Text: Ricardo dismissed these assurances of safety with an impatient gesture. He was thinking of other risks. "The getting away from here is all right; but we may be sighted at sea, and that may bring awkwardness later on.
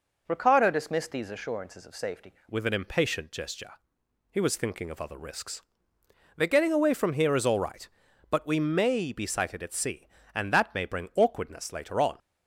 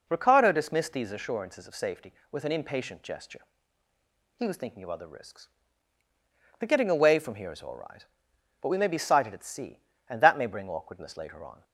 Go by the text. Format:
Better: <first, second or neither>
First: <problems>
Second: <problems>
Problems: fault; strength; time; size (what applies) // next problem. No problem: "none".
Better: second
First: changes voice at "with"; from 2.4 s on; 9.7 s long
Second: none